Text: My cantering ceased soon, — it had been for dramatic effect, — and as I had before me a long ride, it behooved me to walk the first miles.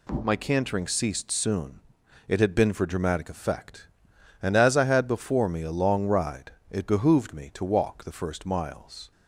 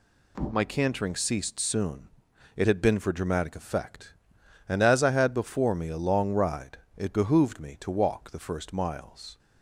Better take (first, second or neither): neither